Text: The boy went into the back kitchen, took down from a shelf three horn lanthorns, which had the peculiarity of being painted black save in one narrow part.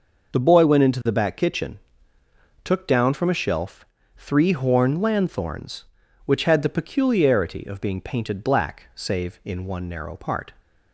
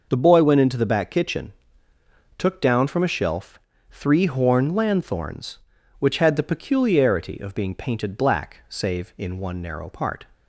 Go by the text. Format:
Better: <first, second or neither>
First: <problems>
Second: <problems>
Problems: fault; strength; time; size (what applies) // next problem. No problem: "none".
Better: neither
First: pauses between "shelf" and "three"; slight; at 3.8 s; 0.32 s long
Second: pauses between "shelf" and "three"; slight; at 3.5 s; 0.32 s long